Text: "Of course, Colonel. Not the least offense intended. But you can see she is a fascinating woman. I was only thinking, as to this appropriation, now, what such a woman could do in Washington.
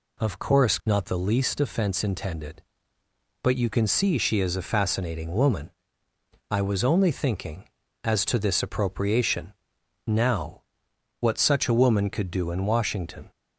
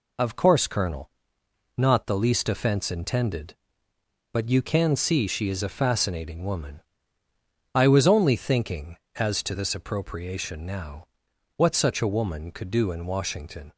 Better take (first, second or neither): second